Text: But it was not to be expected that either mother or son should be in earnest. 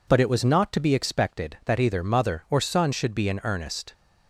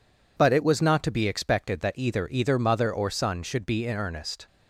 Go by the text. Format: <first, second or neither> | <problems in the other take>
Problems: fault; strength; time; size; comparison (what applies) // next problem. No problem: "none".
first | says "either" twice; at 2.2 s